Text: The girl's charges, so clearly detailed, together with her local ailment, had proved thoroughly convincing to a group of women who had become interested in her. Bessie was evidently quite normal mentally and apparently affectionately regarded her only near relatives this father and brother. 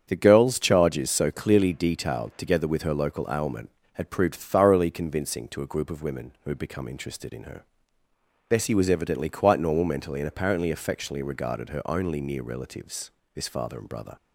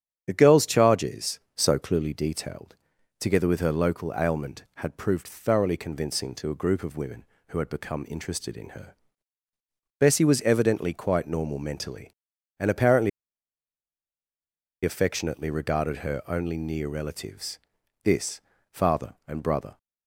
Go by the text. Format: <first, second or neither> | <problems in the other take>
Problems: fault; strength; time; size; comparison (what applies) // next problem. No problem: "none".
first | starts louder than the rest; strong; until 1.2 s; 8.5 dB; strong in the first // pauses between "apparently" and "affectionately"; strong; at 13.0 s; 1.7 s long // pauses between "relatives" and "this"; at 17.5 s; 0.44 s long; slight in the first // pauses between "this" and "father"; slight; at 18.4 s; 0.30 s long